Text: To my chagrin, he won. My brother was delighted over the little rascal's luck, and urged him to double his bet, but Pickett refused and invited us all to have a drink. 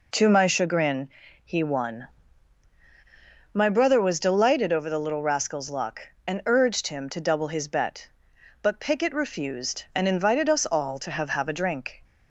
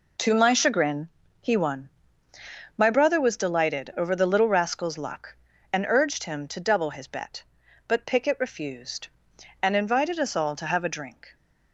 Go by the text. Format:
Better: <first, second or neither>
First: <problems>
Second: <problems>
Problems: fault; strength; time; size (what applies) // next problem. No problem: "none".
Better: second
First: says "have" twice; at 11.2 s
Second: none